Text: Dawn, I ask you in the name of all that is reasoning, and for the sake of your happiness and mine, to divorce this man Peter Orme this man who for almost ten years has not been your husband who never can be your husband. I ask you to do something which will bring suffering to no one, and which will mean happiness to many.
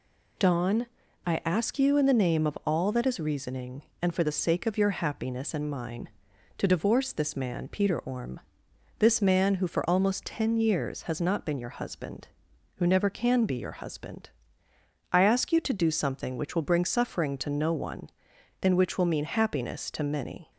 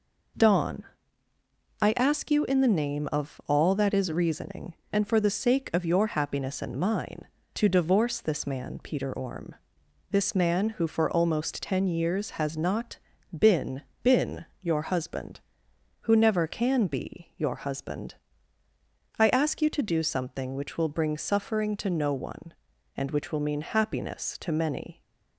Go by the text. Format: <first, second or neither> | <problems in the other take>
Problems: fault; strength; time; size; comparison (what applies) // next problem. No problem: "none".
first | pauses between "Orme" and "this"; noticeable; at 9.5 s; 0.56 s long; noticeable in the first // pauses between "not" and "been"; at 12.9 s; 0.38 s long // says "been" twice; at 14.0 s